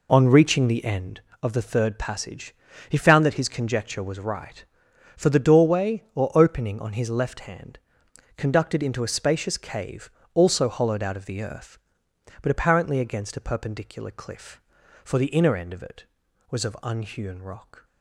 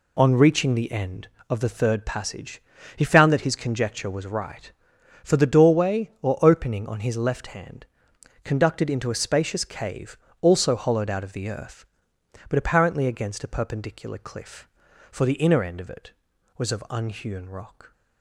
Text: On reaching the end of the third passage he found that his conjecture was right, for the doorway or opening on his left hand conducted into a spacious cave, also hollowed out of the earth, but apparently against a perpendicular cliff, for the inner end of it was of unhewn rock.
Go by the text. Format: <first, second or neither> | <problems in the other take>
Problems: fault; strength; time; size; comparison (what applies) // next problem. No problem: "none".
second | starts louder than the rest; until 1.1 s; 3.5 dB // pauses between "passage" and "he"; slight; at 2.5 s; 0.36 s long; slight in the second // pauses between "hand" and "conducted"; noticeable; at 7.7 s; 0.56 s long; noticeable in the second